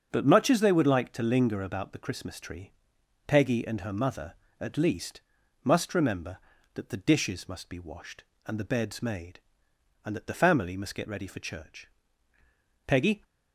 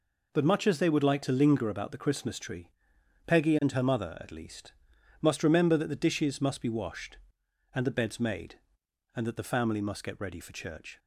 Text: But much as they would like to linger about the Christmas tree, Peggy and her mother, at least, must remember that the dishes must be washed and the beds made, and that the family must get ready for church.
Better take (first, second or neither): second